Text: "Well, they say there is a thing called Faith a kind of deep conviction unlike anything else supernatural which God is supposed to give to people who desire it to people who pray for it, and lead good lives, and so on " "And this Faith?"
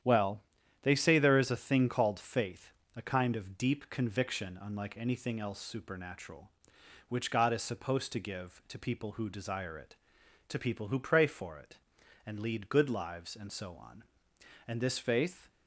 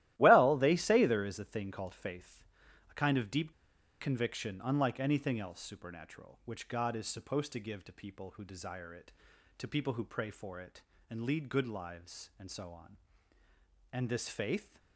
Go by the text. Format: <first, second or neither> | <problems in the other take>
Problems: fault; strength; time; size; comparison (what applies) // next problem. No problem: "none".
first | starts louder than the rest; strong; until 1.1 s; 14.5 dB; strong in the first // pauses between "Faith" and "a"; noticeable; at 2.4 s; 0.46 s long; slight in the first // pauses between "deep" and "conviction"; noticeable; at 3.5 s; 0.49 s long